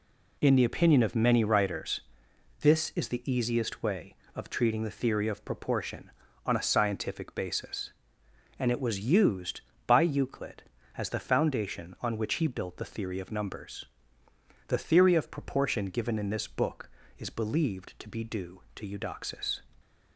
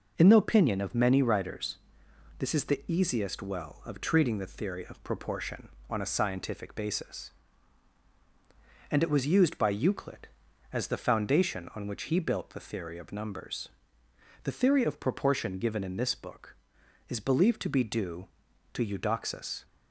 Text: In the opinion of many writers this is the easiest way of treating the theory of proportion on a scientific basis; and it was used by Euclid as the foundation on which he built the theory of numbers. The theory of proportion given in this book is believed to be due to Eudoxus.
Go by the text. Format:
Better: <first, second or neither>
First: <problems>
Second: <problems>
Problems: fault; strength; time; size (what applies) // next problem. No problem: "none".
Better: first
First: pauses between "writers" and "this"; noticeable; at 2.0 s; 0.58 s long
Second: pauses between "writers" and "this"; noticeable; at 1.7 s; 0.64 s long // says "well" for "way"; at 3.4 s